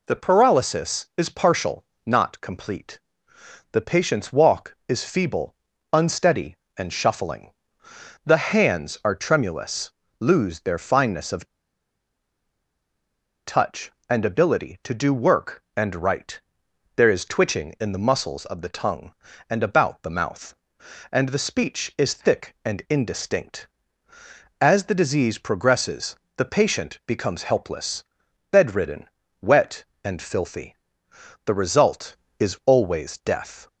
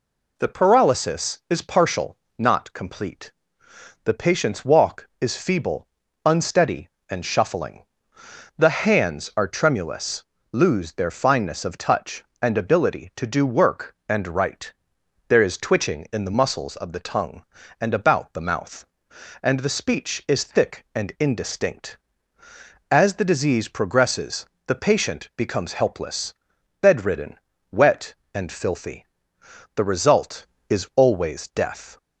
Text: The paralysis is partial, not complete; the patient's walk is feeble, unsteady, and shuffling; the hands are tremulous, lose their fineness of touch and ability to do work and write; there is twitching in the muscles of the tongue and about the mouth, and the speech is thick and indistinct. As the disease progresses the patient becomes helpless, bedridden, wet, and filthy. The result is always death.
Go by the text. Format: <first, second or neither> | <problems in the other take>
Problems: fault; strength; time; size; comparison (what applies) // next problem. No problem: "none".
second | pauses between "of" and "touch"; strong; at 11.4 s; 2.0 s long // pauses between "progresses" and "the"; slight; at 26.1 s; 0.18 s long; slight in the second